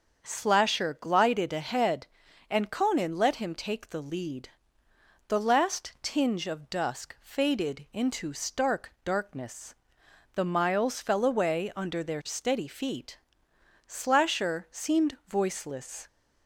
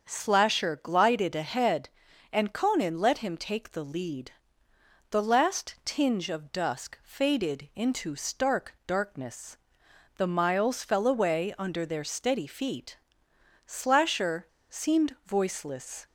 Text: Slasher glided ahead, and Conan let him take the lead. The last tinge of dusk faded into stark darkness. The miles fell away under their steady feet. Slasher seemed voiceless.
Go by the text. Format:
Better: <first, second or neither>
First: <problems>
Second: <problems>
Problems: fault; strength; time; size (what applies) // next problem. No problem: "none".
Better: first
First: starts louder than the rest; until 1.3 s; 7 dB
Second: starts louder than the rest; until 1.1 s; 7 dB // pauses between "Slasher" and "seemed"; slight; at 14.4 s; 0.23 s long